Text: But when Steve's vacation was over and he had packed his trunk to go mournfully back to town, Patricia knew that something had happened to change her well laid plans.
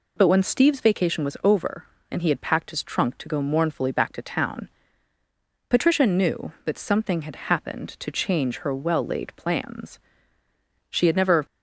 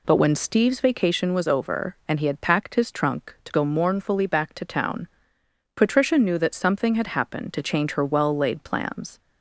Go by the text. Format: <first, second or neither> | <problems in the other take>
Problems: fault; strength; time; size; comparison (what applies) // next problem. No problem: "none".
second | goes on to say "She had never"; from 10.8 s on; 0.56 s long